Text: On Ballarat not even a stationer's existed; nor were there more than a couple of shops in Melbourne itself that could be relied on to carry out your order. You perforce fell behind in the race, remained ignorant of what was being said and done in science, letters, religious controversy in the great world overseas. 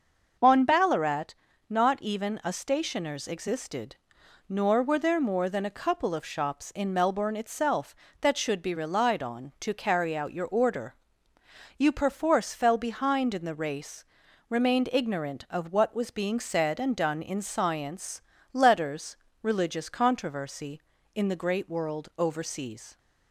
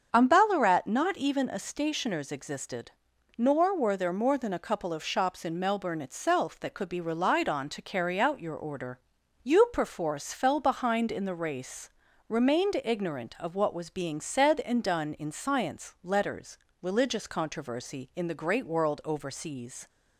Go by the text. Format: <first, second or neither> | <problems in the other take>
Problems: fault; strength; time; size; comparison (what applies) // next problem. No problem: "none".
second | starts louder than the rest; until 1.7 s; 6 dB; also in the second // pauses between "Ballarat" and "not"; slight; at 1.3 s; 0.34 s long // says "should" for "could"; at 8.3 s